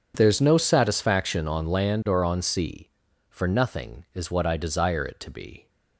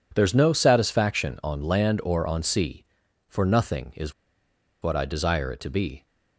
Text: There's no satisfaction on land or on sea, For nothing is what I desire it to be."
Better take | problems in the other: first | pauses between "is" and "what"; noticeable; at 4.1 s; 0.69 s long

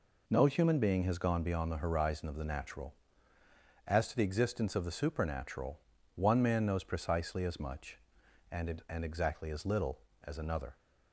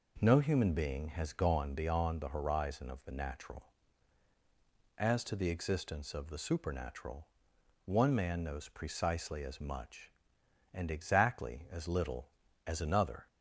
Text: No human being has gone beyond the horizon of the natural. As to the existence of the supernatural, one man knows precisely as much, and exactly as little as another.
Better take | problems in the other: second | says "and" twice; at 8.8 s

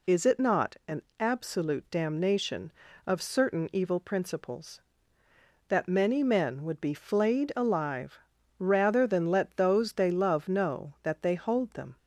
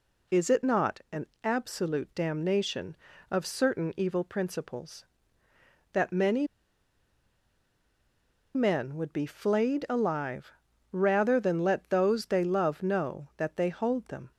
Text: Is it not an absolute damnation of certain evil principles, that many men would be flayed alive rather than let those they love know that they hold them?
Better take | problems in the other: first | pauses between "an" and "absolute"; slight; at 1.2 s; 0.16 s long; slight in the first // pauses between "many" and "men"; strong; at 6.4 s; 2.0 s long // pauses between "alive" and "rather"; at 10.5 s; 0.40 s long; also in the first

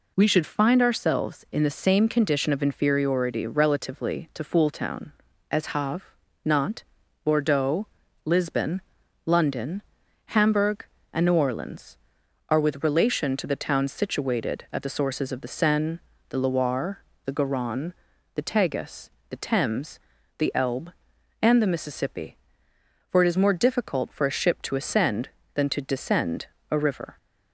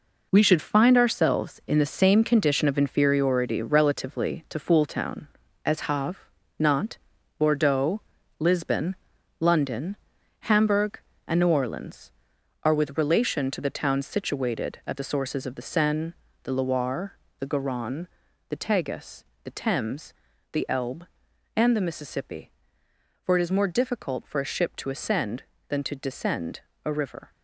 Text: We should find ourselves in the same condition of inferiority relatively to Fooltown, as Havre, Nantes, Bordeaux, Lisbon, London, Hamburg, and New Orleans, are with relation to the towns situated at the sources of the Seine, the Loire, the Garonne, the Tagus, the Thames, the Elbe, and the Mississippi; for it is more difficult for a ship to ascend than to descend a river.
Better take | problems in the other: first | gets quieter; strong; throughout; 8.5 dB // pauses between "descend" and "a"; slight; at 26.6 s; 0.20 s long; slight in the first

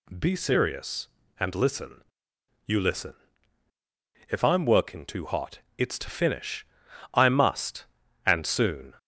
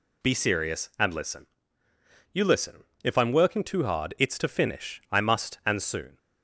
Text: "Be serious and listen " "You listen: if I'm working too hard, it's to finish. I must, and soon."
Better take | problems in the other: second | says "hot" for "hard"; at 5.2 s

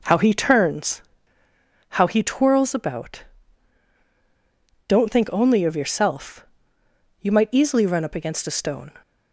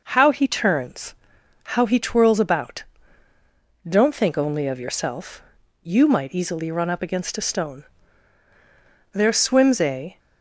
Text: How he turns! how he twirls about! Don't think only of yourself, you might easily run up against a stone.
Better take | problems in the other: first | goes on to say "There swims a"; noticeable; from 9.1 s on; 1.0 s long

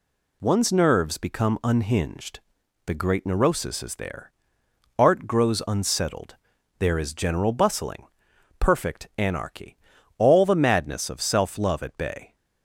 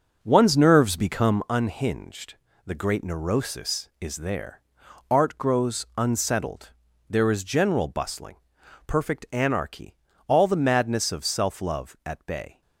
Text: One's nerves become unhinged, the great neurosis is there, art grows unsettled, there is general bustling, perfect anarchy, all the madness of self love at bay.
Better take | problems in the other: first | starts louder than the rest; noticeable; until 1.4 s; 6 dB

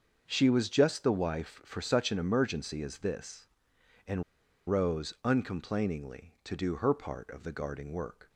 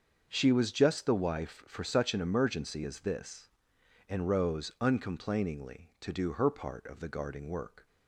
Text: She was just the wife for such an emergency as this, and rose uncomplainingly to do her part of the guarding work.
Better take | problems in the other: second | starts louder than the rest; until 1.2 s; 6.5 dB; also in the second // pauses between "and" and "rose"; at 4.2 s; 0.45 s long

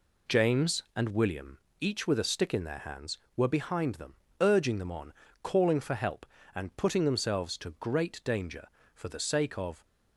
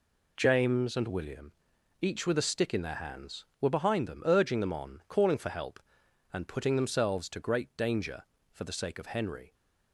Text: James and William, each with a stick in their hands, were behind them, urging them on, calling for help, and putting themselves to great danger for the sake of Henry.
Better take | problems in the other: second | stops before "Henry"; at 9.8 s

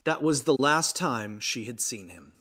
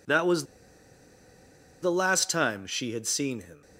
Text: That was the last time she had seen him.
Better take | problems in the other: first | pauses between "was" and "the"; strong; at 0.4 s; 1.3 s long

